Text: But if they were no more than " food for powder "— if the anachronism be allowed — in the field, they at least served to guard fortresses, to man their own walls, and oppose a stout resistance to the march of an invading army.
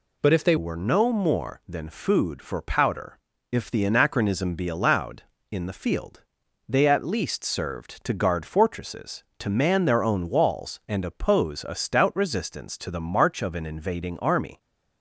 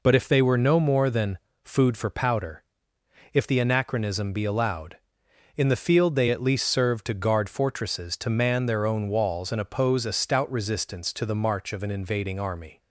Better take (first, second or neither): second